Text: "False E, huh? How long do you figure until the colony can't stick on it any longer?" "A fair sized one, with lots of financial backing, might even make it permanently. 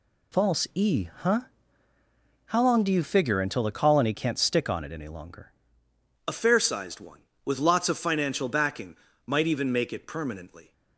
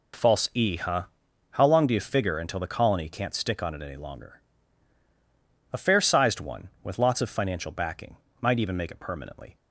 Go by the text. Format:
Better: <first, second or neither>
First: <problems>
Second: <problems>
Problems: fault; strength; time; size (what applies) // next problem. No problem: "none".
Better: second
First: changes voice at "A"; from 6.2 s on; 4.5 s long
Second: none